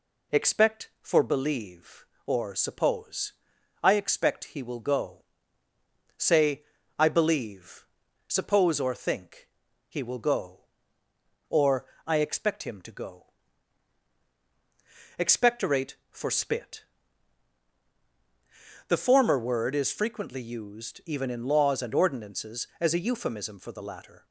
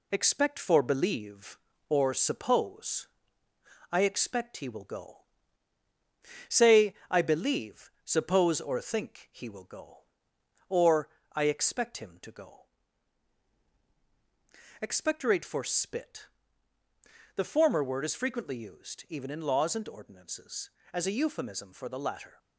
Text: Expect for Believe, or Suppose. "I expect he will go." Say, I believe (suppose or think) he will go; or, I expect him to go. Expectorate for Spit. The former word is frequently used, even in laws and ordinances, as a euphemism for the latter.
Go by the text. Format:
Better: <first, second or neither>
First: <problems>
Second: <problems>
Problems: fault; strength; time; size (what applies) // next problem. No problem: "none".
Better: first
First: none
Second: gets quieter; throughout; 3.5 dB